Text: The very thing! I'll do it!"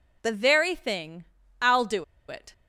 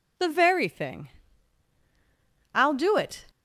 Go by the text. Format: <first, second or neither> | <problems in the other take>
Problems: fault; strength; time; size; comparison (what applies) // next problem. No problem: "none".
second | pauses between "do" and "it"; slight; at 2.0 s; 0.24 s long